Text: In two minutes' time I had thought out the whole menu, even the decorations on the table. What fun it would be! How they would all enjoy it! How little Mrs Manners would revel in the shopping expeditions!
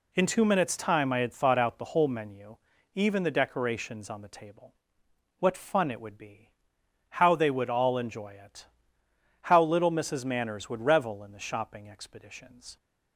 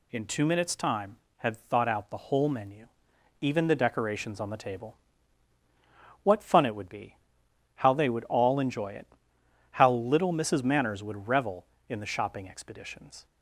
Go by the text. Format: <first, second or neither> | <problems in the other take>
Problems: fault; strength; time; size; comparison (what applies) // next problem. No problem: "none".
first | skips "I"; at 1.2 s